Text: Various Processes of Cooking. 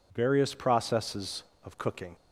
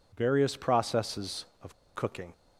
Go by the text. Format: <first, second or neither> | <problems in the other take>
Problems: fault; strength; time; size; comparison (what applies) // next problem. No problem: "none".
first | pauses between "of" and "Cooking"; slight; at 1.7 s; 0.19 s long